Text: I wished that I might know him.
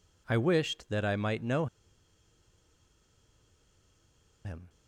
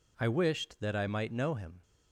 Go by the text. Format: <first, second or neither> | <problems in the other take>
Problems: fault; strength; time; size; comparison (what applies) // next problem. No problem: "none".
second | pauses between "know" and "him"; strong; at 1.6 s; 2.7 s long